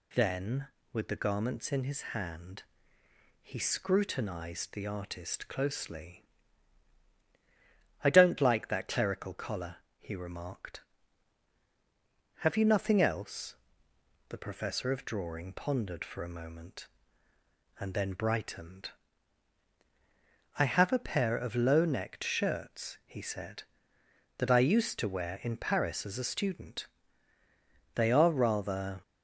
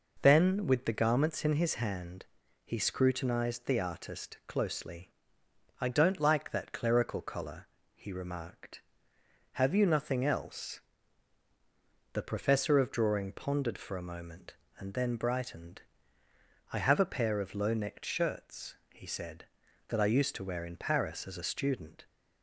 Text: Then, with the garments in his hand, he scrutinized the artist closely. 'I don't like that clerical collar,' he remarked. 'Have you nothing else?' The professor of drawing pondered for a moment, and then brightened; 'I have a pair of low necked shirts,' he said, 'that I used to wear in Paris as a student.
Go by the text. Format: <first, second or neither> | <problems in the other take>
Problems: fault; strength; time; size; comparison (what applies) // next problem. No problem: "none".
second | goes on to say "They are rather"; noticeable; from 27.9 s on; 1.0 s long